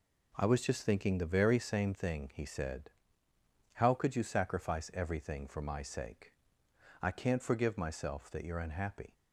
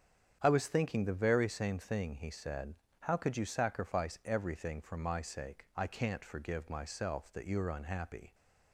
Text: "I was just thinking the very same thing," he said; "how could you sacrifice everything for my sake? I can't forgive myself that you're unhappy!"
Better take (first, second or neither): first